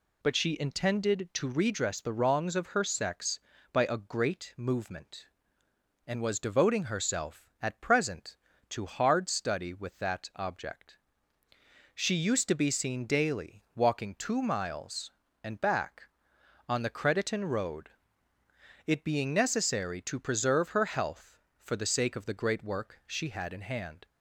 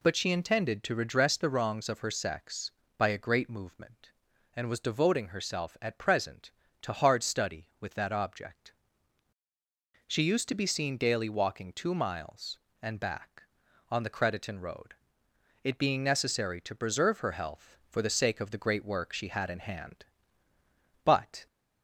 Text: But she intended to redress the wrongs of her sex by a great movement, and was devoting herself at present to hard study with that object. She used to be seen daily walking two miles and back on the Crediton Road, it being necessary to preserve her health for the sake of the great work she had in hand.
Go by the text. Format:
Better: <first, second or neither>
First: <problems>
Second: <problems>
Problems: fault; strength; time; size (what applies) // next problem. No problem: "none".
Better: first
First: none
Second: goes on to say "But"; slight; from 21.0 s on; 0.42 s long